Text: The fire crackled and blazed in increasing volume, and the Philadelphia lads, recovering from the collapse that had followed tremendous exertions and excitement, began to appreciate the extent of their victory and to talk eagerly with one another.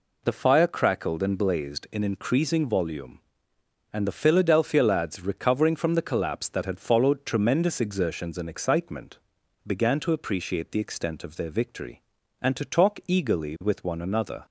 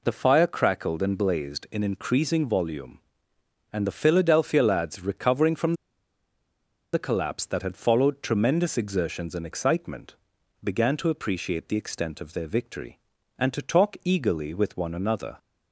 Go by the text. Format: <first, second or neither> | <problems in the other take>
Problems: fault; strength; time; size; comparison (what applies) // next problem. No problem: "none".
first | pauses between "from" and "the"; at 5.7 s; 1.1 s long